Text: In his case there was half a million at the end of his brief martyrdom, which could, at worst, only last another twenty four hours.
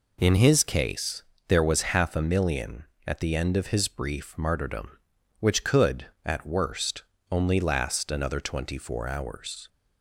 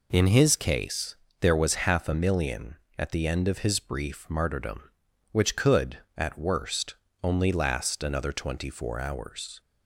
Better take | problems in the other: neither | pauses between "case" and "there"; slight; the same in both

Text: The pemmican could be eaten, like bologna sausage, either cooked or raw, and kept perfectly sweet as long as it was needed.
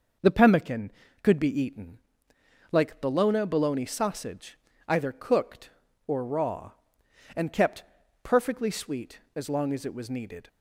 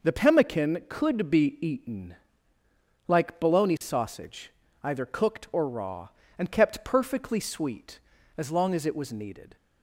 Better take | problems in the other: second | says "bologna" twice; at 3.4 s // pauses between "kept" and "perfectly"; at 7.8 s; 0.40 s long

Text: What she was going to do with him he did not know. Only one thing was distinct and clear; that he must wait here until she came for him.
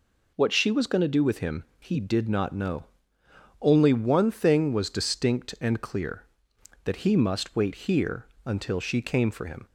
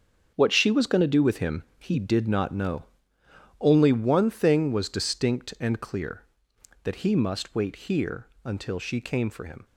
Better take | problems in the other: first | gets quieter; strong; throughout; 10 dB // pauses between "him" and "he"; slight; at 1.6 s; 0.16 s long; slight in the first // pauses between "here" and "until"; slight; at 8.2 s; 0.16 s long; slight in the first

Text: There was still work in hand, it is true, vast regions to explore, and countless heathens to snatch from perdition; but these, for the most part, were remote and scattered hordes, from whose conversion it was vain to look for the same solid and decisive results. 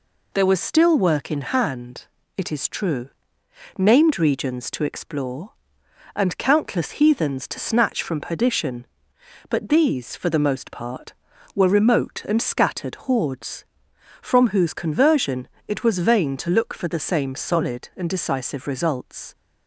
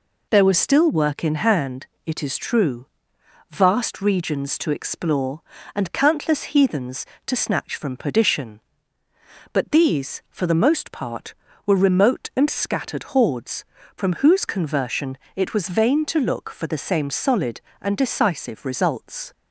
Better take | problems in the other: second | says "named" for "vast"; at 3.7 s // pauses between "conversion" and "it"; slight; at 15.4 s; 0.20 s long; slight in the second

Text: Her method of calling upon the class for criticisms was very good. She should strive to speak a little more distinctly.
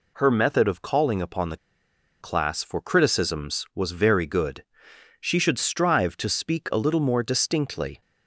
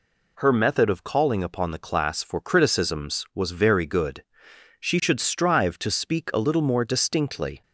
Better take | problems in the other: second | pauses between "the" and "class"; noticeable; at 1.5 s; 0.64 s long

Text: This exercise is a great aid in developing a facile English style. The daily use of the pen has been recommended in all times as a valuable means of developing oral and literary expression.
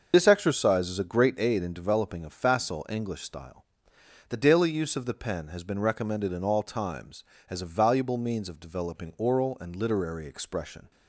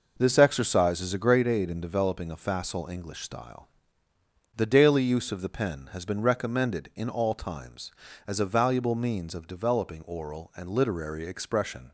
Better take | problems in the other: second | loses the start of "This"; at 0.1 s; 55 ms // starts louder than the rest; until 1.1 s; 6.5 dB

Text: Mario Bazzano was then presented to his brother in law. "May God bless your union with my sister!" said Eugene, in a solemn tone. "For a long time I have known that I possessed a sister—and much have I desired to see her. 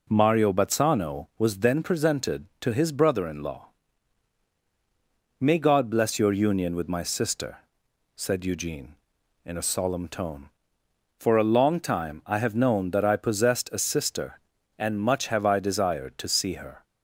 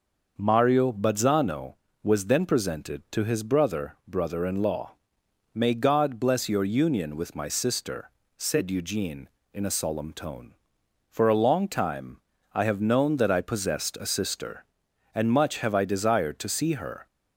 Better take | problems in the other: first | says "brother" twice; at 4.0 s // pauses between "time" and "I"; slight; at 12.1 s; 0.32 s long

